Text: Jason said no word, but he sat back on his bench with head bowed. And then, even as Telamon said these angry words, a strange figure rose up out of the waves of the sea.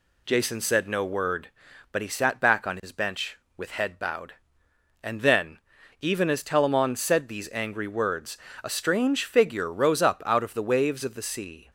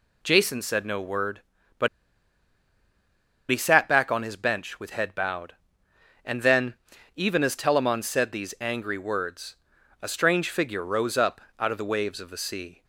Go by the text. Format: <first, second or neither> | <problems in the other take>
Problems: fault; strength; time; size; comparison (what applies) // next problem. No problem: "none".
first | pauses between "but" and "he"; strong; at 1.8 s; 1.6 s long // pauses between "up" and "out"; slight; at 11.4 s; 0.16 s long